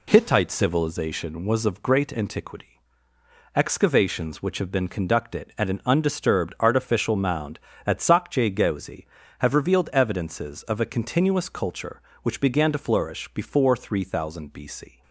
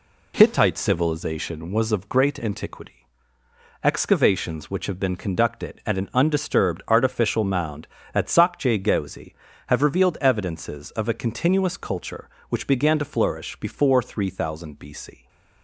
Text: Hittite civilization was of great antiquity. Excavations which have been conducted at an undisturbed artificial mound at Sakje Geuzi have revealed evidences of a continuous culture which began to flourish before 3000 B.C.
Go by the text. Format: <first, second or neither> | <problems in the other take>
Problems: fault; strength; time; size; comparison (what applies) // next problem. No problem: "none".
neither | none